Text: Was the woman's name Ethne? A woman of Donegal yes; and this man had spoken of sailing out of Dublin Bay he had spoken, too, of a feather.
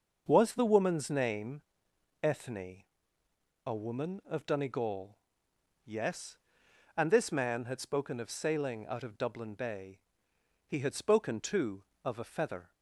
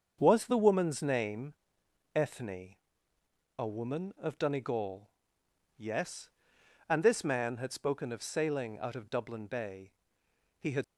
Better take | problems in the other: first | starts louder than the rest; until 1.2 s; 6.5 dB; noticeable in the first // pauses between "name" and "Ethne"; noticeable; at 1.5 s; 0.60 s long; noticeable in the first // pauses between "Donegal" and "yes"; noticeable; at 5.0 s; 0.68 s long; noticeable in the first // pauses between "Bay" and "he"; noticeable; at 9.9 s; 0.68 s long; noticeable in the first // stops before "spoken too of a feather"; at 10.8 s

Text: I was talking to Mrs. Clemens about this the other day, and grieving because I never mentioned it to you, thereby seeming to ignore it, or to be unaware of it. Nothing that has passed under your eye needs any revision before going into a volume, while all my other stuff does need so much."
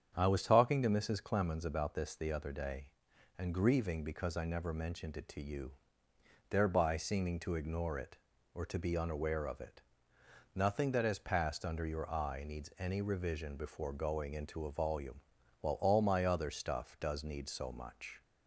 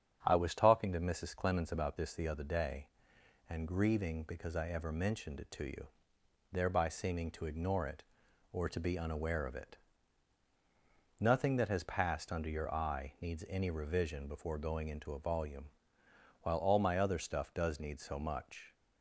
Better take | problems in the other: first | starts louder than the rest; strong; until 1.2 s; 8 dB; strong in the first // says "ever" for "never"; at 4.6 s

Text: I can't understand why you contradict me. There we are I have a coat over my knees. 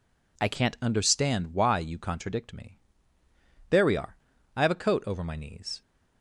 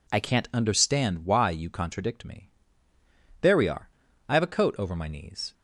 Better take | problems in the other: neither | pauses between "are" and "I"; slight; the same in both

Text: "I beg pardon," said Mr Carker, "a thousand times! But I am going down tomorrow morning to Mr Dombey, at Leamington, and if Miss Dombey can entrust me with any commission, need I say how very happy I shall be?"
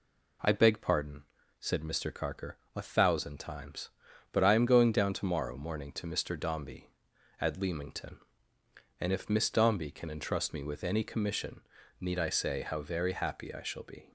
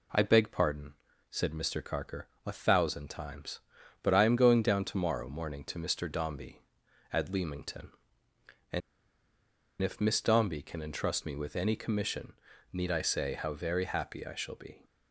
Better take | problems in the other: first | pauses between "and" and "if"; at 8.8 s; 1.0 s long

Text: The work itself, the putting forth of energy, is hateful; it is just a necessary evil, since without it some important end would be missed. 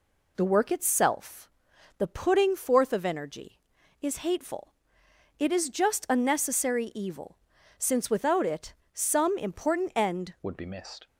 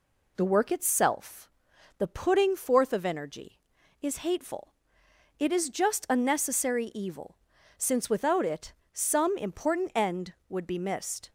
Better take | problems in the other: second | pauses between "it" and "some"; slight; at 8.7 s; 0.18 s long; slight in the second // changes voice at "would"; from 10.4 s on; 0.6 s long

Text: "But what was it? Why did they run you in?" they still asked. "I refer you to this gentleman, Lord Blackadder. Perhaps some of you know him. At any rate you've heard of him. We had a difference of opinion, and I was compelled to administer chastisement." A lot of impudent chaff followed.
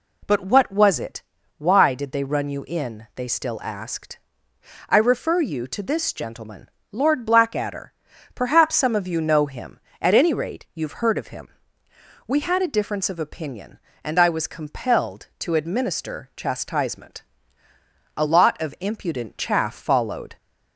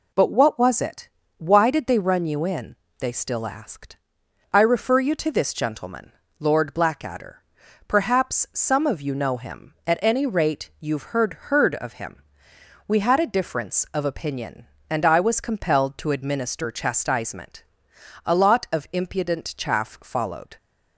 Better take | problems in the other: first | says "heard" twice; at 11.3 s

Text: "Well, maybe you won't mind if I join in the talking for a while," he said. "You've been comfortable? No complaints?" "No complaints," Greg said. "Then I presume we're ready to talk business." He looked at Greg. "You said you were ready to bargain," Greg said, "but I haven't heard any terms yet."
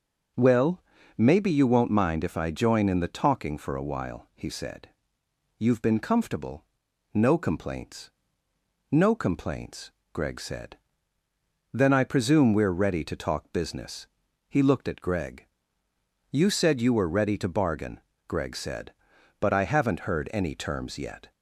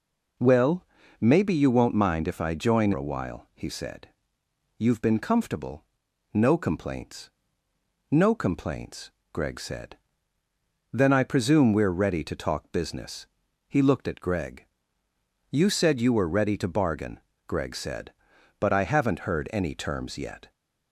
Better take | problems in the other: first | skips "in the talking for"; at 2.9 s

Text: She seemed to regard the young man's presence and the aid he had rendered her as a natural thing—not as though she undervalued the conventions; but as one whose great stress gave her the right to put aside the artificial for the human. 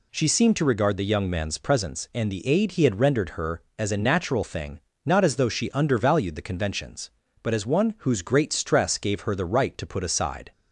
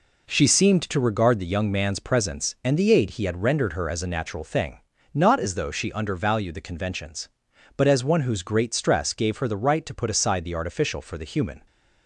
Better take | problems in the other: second | stops before "the artificial for the human"; at 10.5 s

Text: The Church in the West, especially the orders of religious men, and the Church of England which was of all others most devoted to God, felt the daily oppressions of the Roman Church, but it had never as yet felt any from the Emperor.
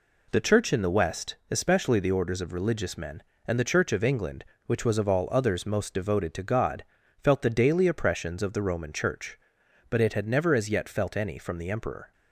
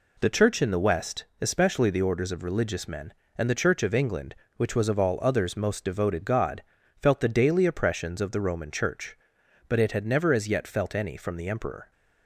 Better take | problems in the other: first | skips "to"; at 6.2 s

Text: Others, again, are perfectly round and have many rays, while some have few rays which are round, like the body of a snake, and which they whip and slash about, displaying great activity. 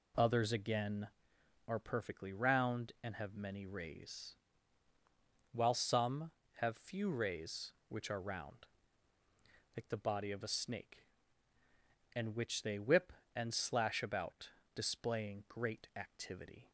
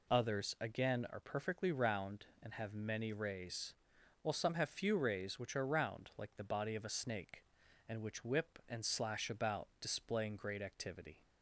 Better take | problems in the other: first | skips "they"; at 8.2 s

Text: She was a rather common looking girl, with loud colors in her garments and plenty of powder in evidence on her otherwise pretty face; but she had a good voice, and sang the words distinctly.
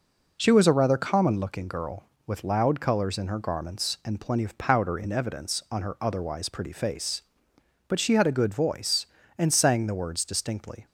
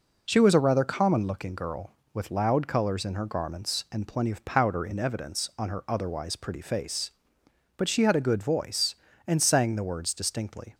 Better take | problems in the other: neither | none

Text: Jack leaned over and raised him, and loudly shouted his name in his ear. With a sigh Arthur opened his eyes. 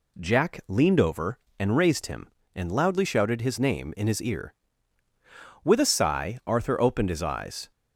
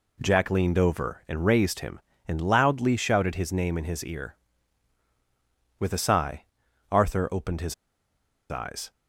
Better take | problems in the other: first | pauses between "sigh" and "Arthur"; noticeable; at 6.4 s; 0.46 s long // pauses between "his" and "eyes"; noticeable; at 7.7 s; 0.75 s long

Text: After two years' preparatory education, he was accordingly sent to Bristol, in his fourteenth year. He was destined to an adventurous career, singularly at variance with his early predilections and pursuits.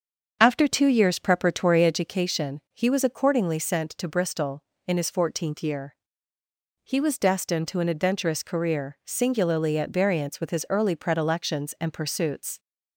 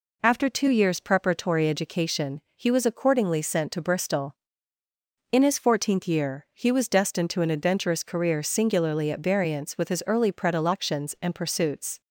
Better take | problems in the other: second | starts louder than the rest; until 2.0 s; 7 dB

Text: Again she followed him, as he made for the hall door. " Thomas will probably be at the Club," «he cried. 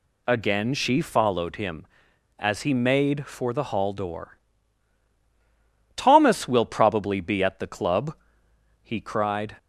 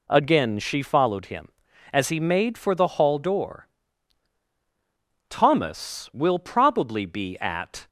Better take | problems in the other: first | stops before "the Club he cried"; at 7.8 s

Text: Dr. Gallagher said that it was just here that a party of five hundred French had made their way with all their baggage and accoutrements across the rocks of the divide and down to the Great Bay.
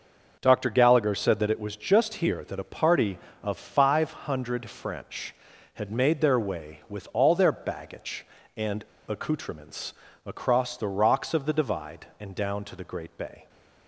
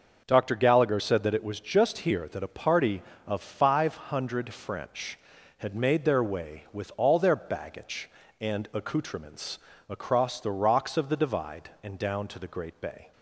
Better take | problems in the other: second | starts louder than the rest; noticeable; until 1.4 s; 6 dB; noticeable in the second // pauses between "and" and "accoutrements"; slight; at 8.8 s; 0.23 s long // pauses between "accoutrements" and "across"; slight; at 9.9 s; 0.32 s long; slight in the second

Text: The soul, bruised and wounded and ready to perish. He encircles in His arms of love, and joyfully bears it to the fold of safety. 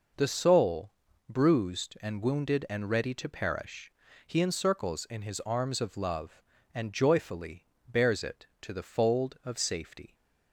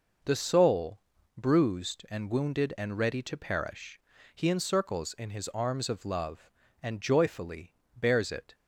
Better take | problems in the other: first | pauses between "joyfully" and "bears"; slight; at 7.7 s; 0.22 s long; slight in the first // stops before "to the fold of safety"; at 8.5 s

